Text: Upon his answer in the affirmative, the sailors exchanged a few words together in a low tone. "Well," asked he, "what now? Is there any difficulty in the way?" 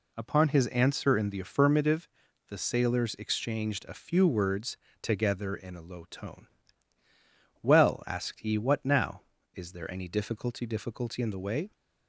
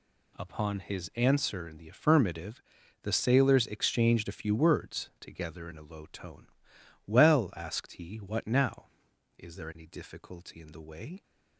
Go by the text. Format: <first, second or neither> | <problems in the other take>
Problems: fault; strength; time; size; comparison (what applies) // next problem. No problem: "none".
second | pauses between "words" and "together"; slight; at 4.7 s; 0.26 s long // says "difficulty" twice; at 10.6 s